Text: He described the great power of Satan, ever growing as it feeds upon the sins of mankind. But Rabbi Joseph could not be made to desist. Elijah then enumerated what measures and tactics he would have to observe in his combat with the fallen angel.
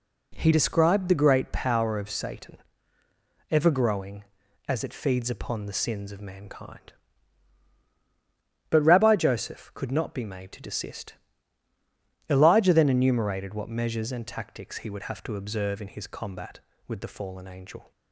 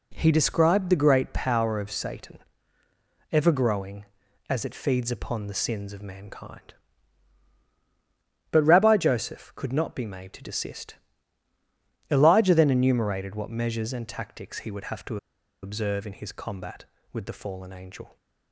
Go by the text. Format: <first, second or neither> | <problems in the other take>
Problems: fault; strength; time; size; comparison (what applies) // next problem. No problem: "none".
first | pauses between "to" and "observe"; noticeable; at 15.1 s; 0.46 s long